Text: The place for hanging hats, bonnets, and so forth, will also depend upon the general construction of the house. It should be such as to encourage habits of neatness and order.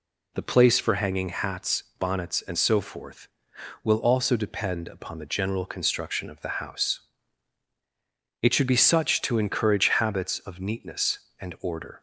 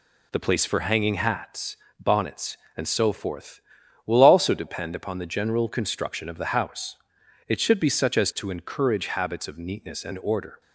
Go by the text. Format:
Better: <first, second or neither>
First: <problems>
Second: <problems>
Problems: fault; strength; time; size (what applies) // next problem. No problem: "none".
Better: second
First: skips "as"; at 9.2 s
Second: none